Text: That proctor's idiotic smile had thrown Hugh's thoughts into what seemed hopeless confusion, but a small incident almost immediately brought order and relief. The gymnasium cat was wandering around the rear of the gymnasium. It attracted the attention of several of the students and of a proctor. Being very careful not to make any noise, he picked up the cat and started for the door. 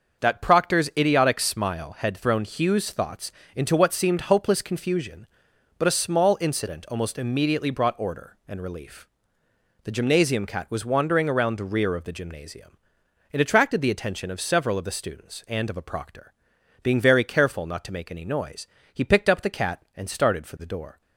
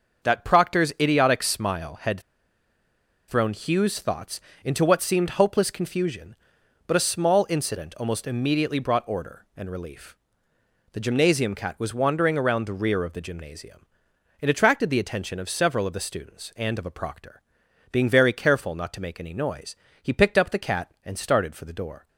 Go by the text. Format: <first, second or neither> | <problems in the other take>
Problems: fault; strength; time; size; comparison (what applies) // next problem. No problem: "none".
first | starts louder than the rest; until 1.3 s; 6.5 dB; also in the first // pauses between "had" and "thrown"; at 2.1 s; 1.0 s long // pauses between "thoughts" and "into"; slight; at 4.3 s; 0.24 s long; slight in the first